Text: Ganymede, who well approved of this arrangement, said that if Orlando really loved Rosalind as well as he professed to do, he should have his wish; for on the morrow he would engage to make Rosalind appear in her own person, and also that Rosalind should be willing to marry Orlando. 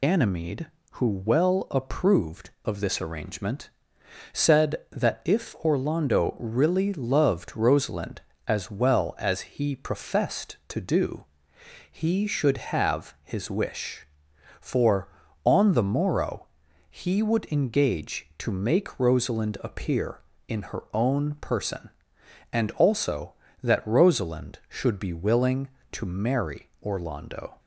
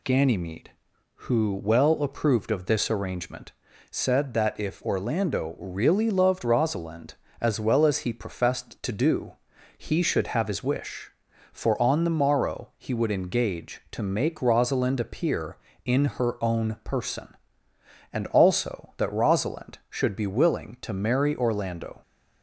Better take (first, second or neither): second